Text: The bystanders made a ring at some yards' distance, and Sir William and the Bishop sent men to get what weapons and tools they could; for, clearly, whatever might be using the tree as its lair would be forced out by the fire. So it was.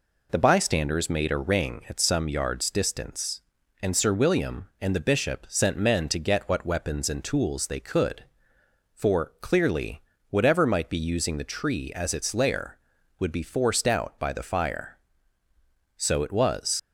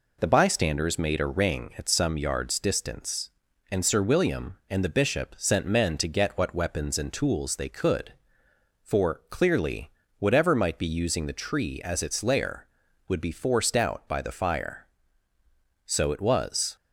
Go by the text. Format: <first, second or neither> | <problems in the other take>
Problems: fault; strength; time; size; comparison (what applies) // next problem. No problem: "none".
second | leaves "was" unfinished; at 16.7 s; 65 ms